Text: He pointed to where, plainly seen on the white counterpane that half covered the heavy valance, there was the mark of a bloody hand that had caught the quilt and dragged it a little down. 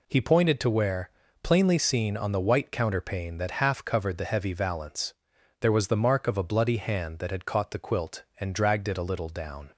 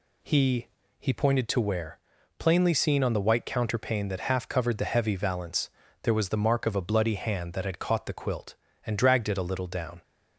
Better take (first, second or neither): first